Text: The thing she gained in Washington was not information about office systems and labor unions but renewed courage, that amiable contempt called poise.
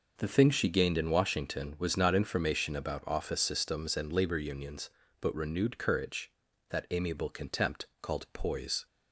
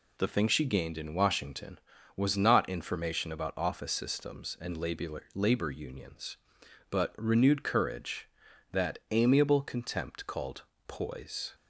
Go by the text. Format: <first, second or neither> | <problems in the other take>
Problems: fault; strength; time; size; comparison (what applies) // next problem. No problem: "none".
first | says "labor" twice; at 5.3 s // pauses between "called" and "poise"; slight; at 10.6 s; 0.24 s long